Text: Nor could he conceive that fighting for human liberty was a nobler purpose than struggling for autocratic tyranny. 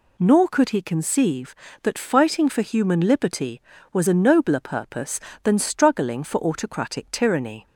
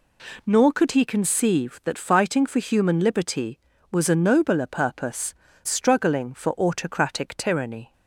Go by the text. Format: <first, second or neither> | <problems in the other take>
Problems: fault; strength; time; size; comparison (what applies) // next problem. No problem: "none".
first | skips "than"; at 5.4 s